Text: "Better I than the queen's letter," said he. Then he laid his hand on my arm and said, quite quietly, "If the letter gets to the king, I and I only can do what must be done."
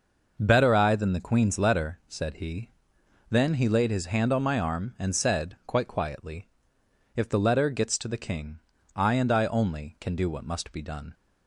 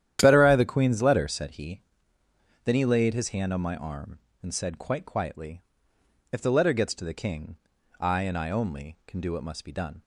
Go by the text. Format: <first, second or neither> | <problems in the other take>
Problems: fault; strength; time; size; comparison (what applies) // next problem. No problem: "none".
first | starts louder than the rest; strong; until 1.2 s; 11 dB // skips "than"; at 0.5 s